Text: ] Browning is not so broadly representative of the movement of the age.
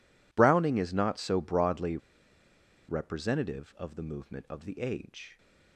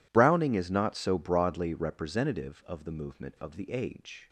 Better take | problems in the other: second | pauses between "broadly" and "representative"; noticeable; at 1.9 s; 0.91 s long

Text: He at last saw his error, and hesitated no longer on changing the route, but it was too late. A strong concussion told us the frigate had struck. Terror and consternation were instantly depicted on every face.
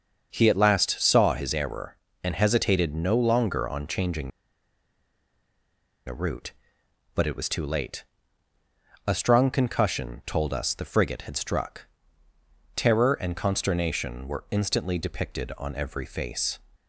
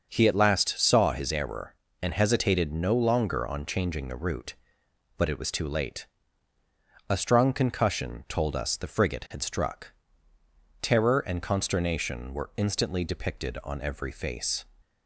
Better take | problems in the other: second | starts louder than the rest; until 1.3 s; 6.5 dB; also in the second // pauses between "changing" and "the"; strong; at 4.2 s; 1.7 s long

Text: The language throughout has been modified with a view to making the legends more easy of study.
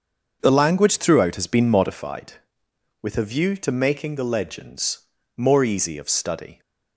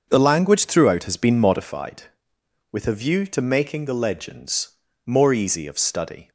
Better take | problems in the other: neither | starts louder than the rest; the same in both // pauses between "legends" and "more"; slight; the same in both

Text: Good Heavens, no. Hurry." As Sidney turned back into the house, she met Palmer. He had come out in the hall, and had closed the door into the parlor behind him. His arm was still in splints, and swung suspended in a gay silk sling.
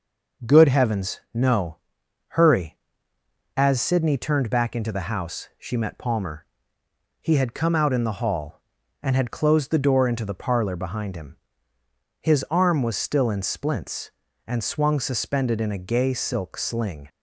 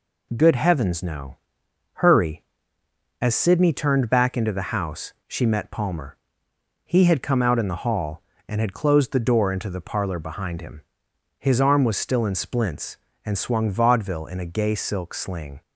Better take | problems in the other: first | says "vaudeville" for "suspended"; at 13.7 s

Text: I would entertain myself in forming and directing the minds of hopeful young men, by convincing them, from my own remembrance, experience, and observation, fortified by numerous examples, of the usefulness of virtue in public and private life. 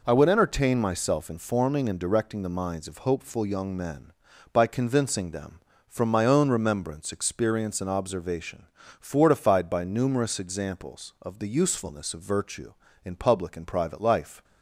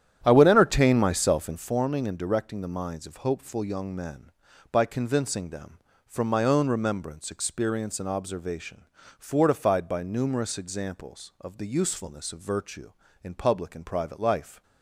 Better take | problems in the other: first | starts louder than the rest; strong; until 1.8 s; 10 dB

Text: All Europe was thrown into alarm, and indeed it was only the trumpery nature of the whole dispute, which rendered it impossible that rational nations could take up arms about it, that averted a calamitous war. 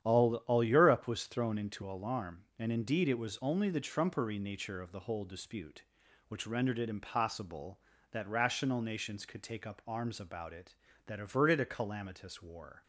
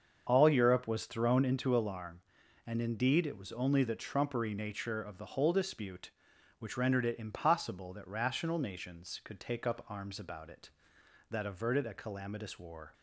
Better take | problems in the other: second | starts louder than the rest; strong; until 1.1 s; 9.5 dB; also in the second // says "All" twice; at 0.4 s

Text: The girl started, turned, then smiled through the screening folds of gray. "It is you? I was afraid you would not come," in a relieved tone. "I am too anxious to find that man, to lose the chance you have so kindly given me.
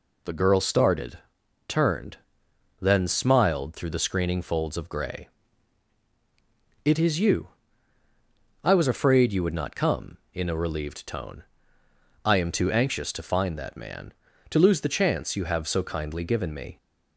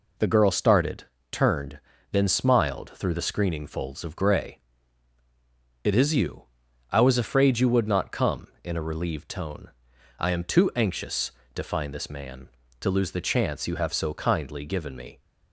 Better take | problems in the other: first | says "this" for "that"; at 11.9 s

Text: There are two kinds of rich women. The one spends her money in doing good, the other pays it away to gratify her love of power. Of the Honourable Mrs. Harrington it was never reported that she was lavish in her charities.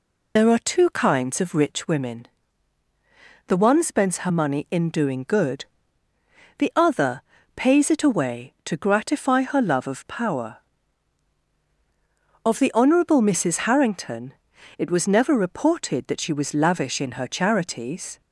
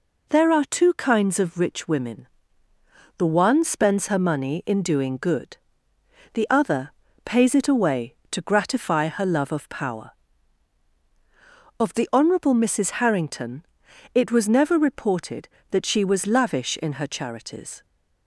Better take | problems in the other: second | loses the start of "There"; at 0.3 s; 40 ms // pauses between "other" and "pays"; slight; at 7.2 s; 0.34 s long; slight in the second // pauses between "Harrington" and "it"; noticeable; at 14.3 s; 0.46 s long; noticeable in the second

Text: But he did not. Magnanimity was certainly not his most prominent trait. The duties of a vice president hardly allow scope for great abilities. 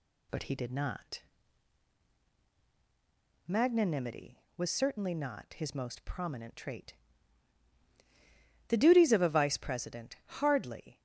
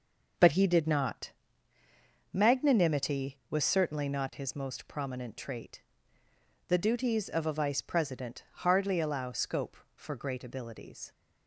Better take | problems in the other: second | stops before "allow scope for great abilities"; at 10.9 s

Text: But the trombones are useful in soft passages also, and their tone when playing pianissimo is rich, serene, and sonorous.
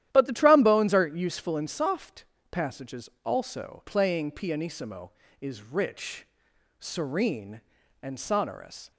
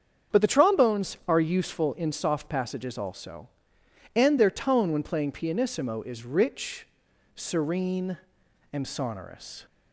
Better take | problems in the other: second | starts louder than the rest; strong; until 1.1 s; 12 dB; strong in the second // pauses between "soft" and "passages"; slight; at 2.2 s; 0.26 s long // pauses between "passages" and "also"; slight; at 3.0 s; 0.16 s long // skips "and their tone when"; at 3.8 s

